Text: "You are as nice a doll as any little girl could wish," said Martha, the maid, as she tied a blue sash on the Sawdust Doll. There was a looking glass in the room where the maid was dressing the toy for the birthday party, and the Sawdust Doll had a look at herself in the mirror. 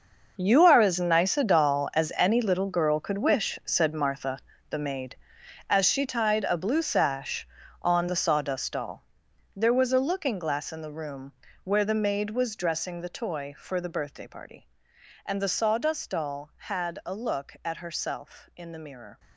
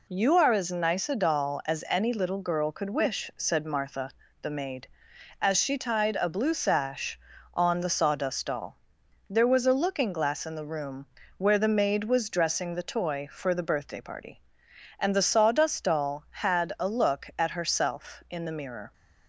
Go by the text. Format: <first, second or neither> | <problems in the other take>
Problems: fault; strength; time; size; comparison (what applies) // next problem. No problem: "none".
second | gets quieter; strong; throughout; 14.5 dB // pauses between "room" and "where"; slight; at 11.3 s; 0.28 s long; slight in the second